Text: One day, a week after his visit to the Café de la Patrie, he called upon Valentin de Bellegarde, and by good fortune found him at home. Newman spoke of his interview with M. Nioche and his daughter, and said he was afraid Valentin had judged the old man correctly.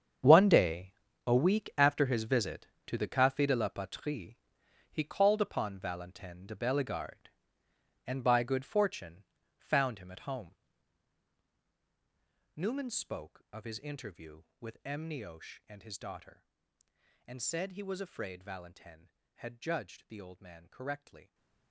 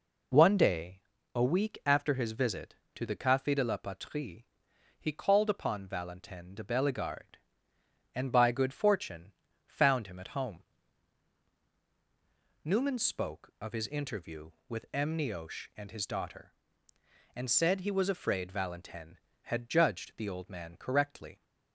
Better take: second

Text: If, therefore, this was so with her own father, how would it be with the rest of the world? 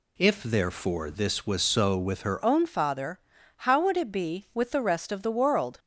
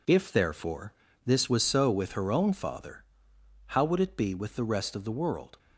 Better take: second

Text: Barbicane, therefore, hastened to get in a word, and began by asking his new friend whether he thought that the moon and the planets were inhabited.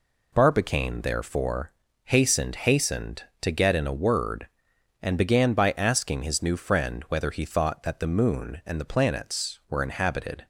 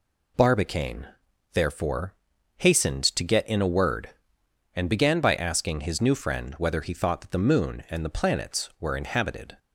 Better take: second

